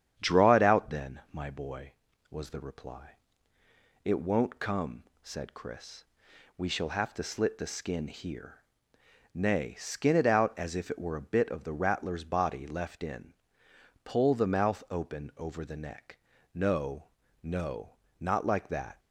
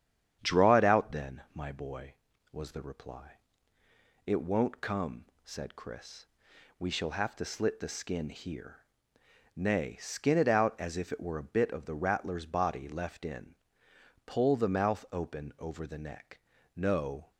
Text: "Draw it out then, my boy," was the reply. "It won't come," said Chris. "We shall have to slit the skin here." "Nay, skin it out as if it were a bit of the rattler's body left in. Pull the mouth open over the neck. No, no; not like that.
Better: first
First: starts louder than the rest; strong; until 1.1 s; 9 dB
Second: starts louder than the rest; strong; until 1.4 s; 9 dB // stops before "no not like that"; at 17.3 s

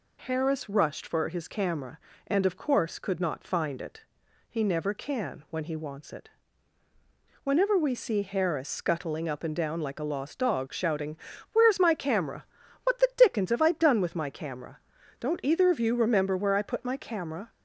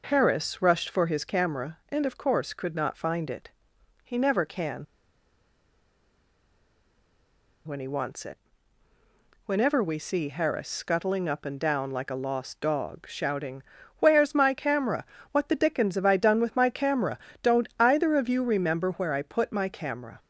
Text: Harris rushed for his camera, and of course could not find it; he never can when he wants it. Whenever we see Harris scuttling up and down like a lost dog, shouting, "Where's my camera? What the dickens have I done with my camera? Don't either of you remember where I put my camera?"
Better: first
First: none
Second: pauses between "can" and "when"; strong; at 4.8 s; 2.8 s long

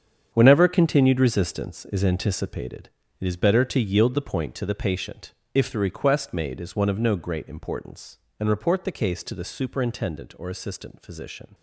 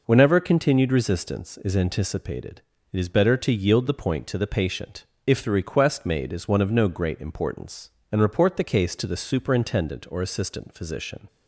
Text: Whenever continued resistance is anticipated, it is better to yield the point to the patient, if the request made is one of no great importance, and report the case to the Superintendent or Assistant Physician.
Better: second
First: gets quieter; strong; throughout; 11.5 dB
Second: none

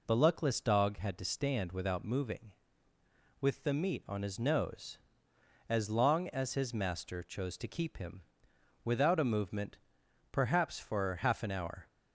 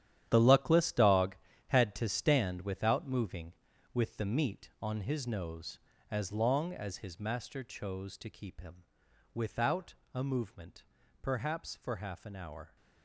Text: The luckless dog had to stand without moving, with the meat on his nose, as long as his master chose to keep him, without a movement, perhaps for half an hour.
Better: first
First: none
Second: gets quieter; strong; throughout; 12.5 dB // pauses between "without" and "a"; slight; at 9.9 s; 0.20 s long

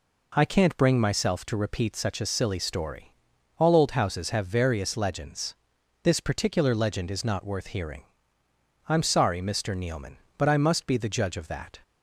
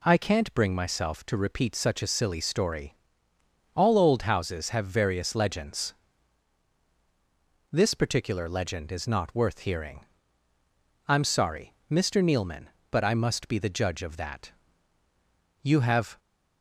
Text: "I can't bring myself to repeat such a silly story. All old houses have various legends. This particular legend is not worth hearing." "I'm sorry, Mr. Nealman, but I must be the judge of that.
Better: first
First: none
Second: goes on to say "You have"; from 15.6 s on; 0.56 s long

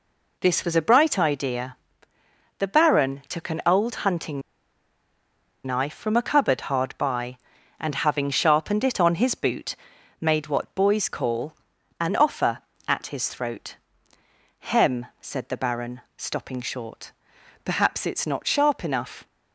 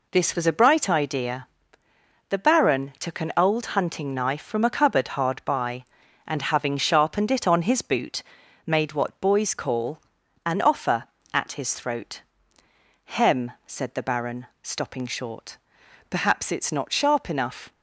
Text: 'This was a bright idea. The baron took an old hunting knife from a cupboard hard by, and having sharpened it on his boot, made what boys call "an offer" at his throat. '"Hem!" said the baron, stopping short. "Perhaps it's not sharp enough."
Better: second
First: pauses between "hunting" and "knife"; at 4.4 s; 1.2 s long // pauses between "call" and "an"; noticeable; at 11.5 s; 0.46 s long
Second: pauses between "call" and "an"; noticeable; at 9.9 s; 0.46 s long

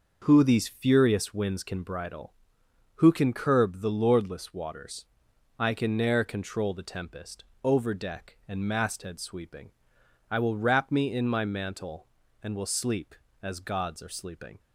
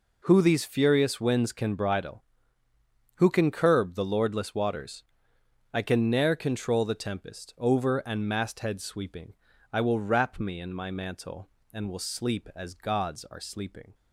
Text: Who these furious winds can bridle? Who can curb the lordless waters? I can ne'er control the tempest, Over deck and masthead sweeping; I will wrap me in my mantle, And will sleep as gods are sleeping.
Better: first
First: none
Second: skips "deck"; at 8.0 s

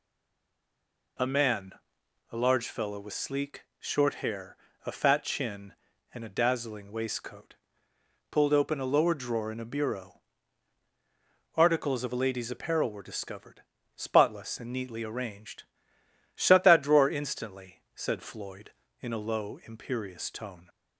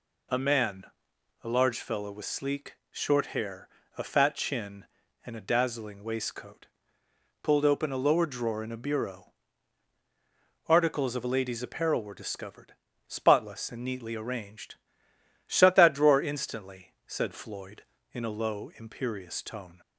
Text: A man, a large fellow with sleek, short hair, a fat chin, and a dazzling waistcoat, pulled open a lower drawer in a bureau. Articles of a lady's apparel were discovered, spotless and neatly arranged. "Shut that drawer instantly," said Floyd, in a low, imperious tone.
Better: second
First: stays silent before the first word; noticeable; until 1.1 s; 1.1 s long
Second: none

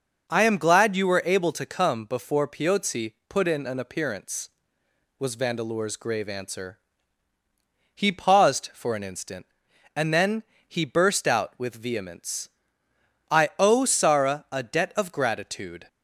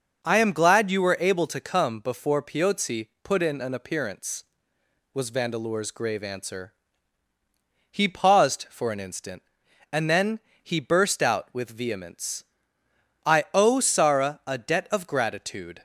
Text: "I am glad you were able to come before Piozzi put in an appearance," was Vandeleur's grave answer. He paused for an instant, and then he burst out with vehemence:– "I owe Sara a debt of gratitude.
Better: neither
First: pauses between "Piozzi" and "put"; slight; at 3.1 s; 0.16 s long // pauses between "then" and "he"; slight; at 10.4 s; 0.22 s long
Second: pauses between "Piozzi" and "put"; slight; at 3.0 s; 0.16 s long // pauses between "then" and "he"; slight; at 10.3 s; 0.22 s long

